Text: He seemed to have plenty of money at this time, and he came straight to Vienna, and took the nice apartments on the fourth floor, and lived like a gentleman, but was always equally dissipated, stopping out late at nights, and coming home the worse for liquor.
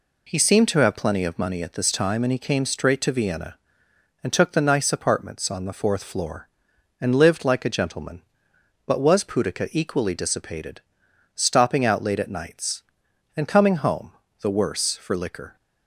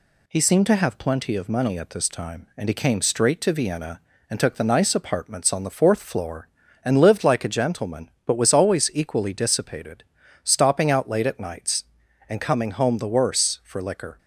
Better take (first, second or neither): second